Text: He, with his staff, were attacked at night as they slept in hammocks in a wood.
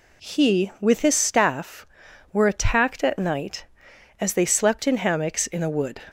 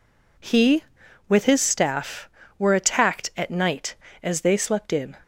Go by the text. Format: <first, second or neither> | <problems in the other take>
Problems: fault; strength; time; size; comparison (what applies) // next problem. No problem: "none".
first | stops before "hammocks in a wood"; at 5.2 s